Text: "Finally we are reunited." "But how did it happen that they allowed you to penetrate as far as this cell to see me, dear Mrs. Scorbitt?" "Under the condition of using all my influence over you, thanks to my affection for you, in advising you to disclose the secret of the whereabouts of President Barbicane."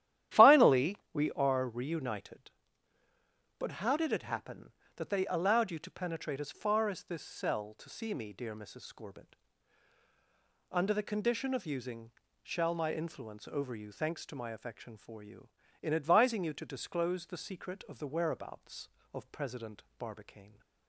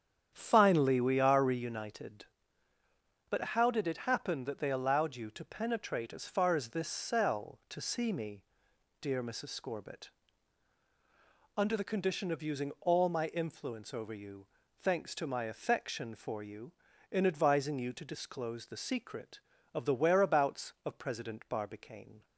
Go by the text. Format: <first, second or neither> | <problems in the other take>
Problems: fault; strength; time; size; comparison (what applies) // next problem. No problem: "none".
second | starts louder than the rest; strong; until 1.5 s; 11.5 dB; strong in the second // pauses between "Finally" and "we"; slight; at 0.9 s; 0.16 s long // says "shall" for "all"; at 12.4 s // pauses between "President" and "Barbicane"; slight; at 19.8 s; 0.16 s long